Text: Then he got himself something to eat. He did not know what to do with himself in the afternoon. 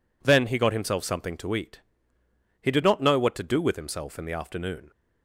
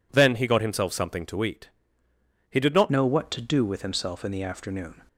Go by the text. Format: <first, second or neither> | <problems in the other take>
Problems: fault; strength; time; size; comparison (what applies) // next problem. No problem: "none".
first | changes voice at "know"; from 2.9 s on; 2.1 s long